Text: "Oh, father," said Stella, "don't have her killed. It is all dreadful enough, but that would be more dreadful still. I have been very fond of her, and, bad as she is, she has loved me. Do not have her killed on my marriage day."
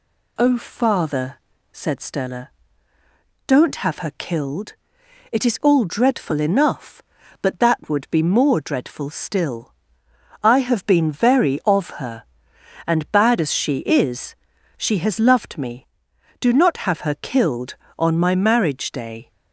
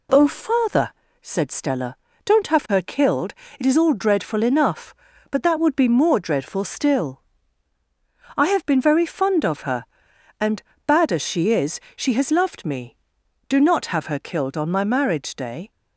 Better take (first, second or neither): second